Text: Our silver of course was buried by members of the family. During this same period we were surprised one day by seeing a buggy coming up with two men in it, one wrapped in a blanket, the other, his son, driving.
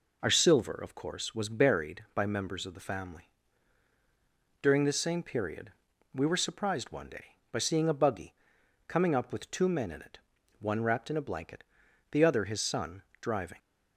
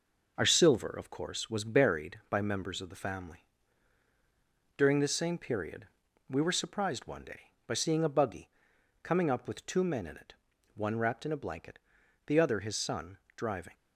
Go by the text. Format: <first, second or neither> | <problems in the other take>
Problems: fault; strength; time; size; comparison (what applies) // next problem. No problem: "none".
first | gets quieter; noticeable; throughout; 4 dB // pauses between "period" and "we"; at 5.8 s; 0.42 s long; also in the first // pauses between "buggy" and "coming"; noticeable; at 8.4 s; 0.54 s long; noticeable in the first